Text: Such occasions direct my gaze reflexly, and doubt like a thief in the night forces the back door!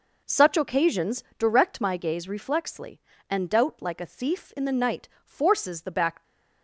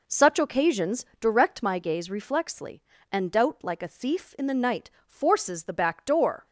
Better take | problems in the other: second | pauses between "night" and "forces"; slight; at 5.0 s; 0.16 s long; slight in the second // stops before "door"; at 6.2 s

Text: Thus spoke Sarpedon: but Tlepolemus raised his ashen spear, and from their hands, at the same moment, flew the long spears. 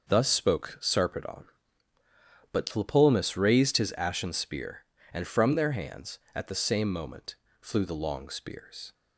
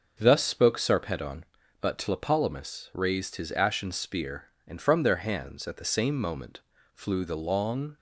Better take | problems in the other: first | starts louder than the rest; noticeable; until 1.1 s; 6 dB; also in the first // stops before "spears"; at 7.9 s

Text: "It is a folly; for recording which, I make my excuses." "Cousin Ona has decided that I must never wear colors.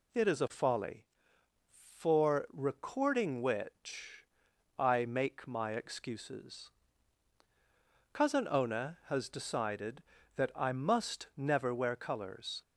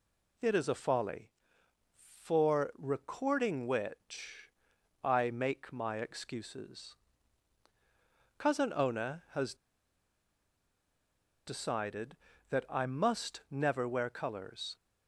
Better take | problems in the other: first | pauses between "has" and "decided"; strong; at 9.5 s; 1.9 s long

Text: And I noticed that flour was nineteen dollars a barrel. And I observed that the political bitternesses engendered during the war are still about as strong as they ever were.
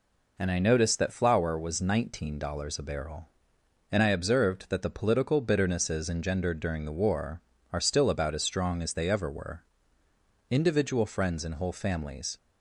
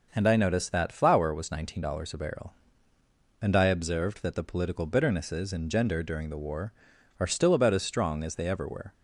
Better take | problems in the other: second | goes on to say "Individual friends and whole families"; strong; from 10.4 s on; 1.8 s long

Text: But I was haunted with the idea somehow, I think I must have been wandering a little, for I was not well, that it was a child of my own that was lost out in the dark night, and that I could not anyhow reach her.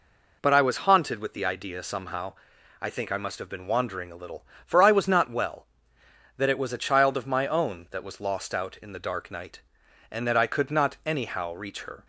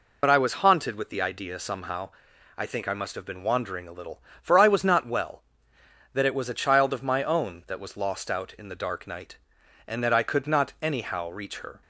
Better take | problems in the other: first | loses the start of "But"; at 0.2 s; 60 ms

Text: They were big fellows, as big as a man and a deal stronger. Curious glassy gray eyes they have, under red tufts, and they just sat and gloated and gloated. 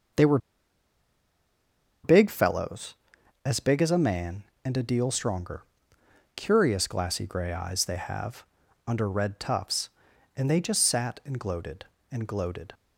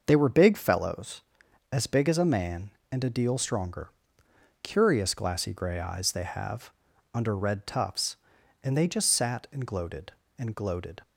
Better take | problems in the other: second | starts louder than the rest; until 2.8 s; 6 dB; also in the second // pauses between "were" and "big"; strong; at 0.3 s; 1.6 s long

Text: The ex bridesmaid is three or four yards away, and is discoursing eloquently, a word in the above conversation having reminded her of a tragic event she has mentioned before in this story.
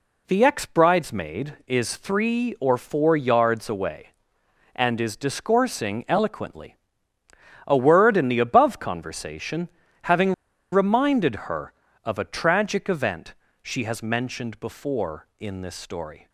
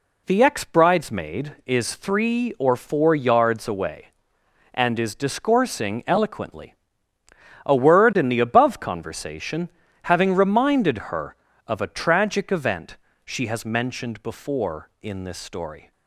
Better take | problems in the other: second | pauses between "conversation" and "having"; slight; at 9.6 s; 0.36 s long; slight in the second // pauses between "having" and "reminded"; at 10.3 s; 0.39 s long // pauses between "reminded" and "her"; slight; at 11.3 s; 0.16 s long; slight in the second // pauses between "event" and "she"; slight; at 13.3 s; 0.28 s long; slight in the second

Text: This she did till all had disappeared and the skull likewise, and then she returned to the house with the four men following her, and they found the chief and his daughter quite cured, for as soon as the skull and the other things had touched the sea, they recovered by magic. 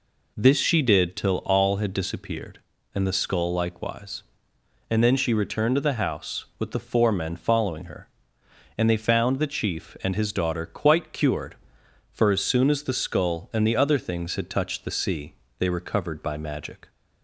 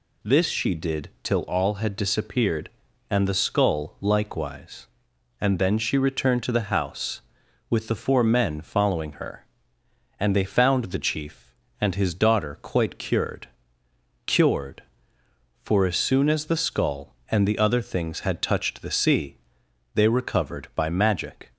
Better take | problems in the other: first | says "cured" twice; at 14.2 s

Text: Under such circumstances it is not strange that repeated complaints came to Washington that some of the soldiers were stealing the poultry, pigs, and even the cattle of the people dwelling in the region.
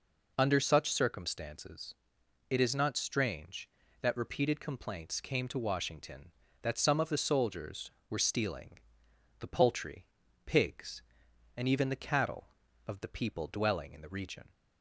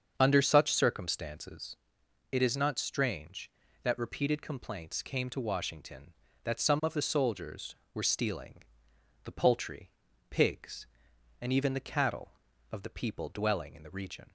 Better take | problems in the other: first | starts louder than the rest; until 1.9 s; 7 dB // pauses between "circumstances" and "it"; noticeable; at 1.7 s; 0.56 s long; noticeable in the first // pauses between "stealing" and "the"; noticeable; at 8.6 s; 0.62 s long; noticeable in the first

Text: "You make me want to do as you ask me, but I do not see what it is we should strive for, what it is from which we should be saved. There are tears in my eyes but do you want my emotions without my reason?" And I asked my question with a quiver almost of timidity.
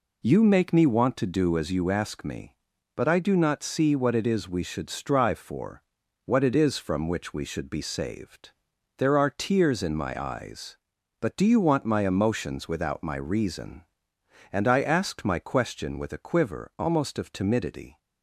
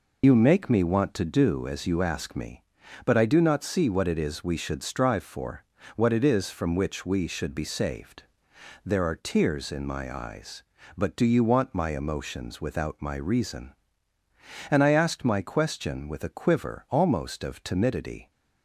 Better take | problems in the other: first | loses the start of "You"; at 0.2 s; 55 ms

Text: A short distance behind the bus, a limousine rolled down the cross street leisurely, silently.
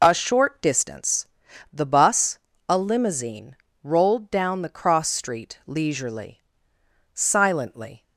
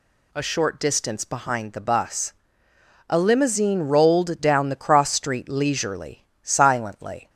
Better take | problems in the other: second | skips "behind"; at 1.4 s // pauses between "limousine" and "rolled"; slight; at 3.5 s; 0.30 s long

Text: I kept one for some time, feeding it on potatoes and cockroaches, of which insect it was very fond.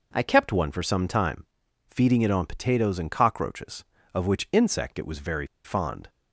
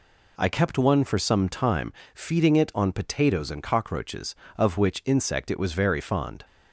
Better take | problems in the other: second | pauses between "very" and "fond"; slight; at 5.4 s; 0.18 s long

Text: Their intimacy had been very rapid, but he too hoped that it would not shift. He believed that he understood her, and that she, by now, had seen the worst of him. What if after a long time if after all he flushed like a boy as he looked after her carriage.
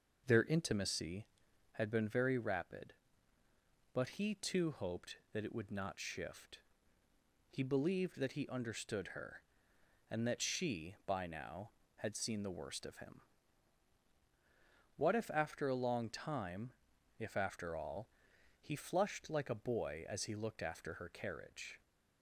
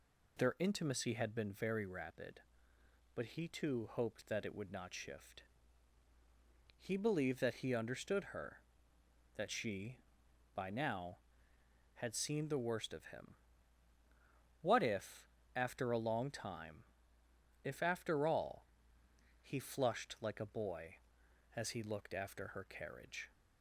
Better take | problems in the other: first | skips "and"; at 8.9 s // pauses between "if" and "after"; slight; at 15.2 s; 0.28 s long // pauses between "time" and "if"; noticeable; at 16.8 s; 0.80 s long; noticeable in the first // pauses between "all" and "he"; noticeable; at 18.6 s; 0.74 s long; noticeable in the first

